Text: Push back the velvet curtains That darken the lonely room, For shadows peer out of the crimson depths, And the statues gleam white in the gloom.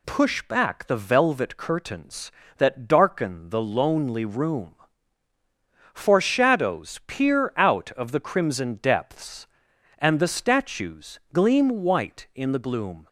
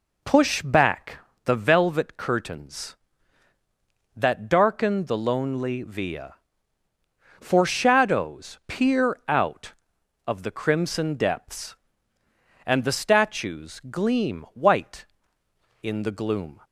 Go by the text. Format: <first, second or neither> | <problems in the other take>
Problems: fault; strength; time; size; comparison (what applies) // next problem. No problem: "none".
first | pauses between "back" and "the"; slight; at 1.1 s; 0.26 s long // says "via" for "room"; at 5.8 s